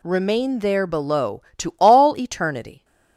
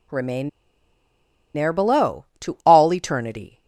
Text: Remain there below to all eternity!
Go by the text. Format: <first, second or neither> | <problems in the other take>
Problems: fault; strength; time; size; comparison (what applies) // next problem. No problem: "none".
first | pauses between "Remain" and "there"; at 0.4 s; 1.0 s long